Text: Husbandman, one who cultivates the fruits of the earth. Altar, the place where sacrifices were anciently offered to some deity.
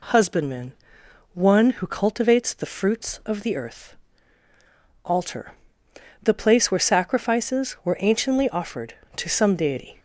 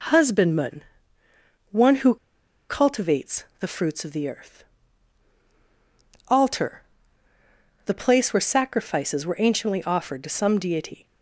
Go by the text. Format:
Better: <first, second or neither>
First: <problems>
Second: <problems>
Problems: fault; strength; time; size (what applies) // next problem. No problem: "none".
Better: first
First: none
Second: pauses between "who" and "cultivates"; noticeable; at 2.1 s; 0.53 s long